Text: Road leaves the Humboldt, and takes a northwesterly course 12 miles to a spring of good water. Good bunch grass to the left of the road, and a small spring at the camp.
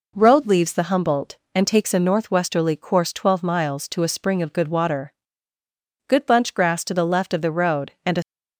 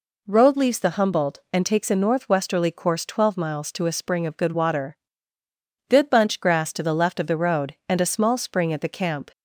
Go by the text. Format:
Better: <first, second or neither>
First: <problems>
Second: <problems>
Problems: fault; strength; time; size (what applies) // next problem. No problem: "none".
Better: second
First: stops before "small spring at the camp"; at 8.2 s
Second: none